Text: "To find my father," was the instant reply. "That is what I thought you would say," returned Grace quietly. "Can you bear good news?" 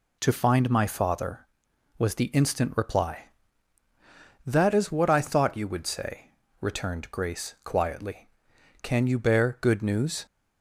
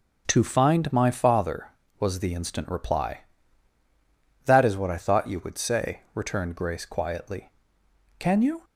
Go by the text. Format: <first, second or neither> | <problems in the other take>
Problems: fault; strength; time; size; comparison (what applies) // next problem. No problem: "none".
first | starts louder than the rest; noticeable; until 1.2 s; 6 dB // stops before "bear good news"; at 8.6 s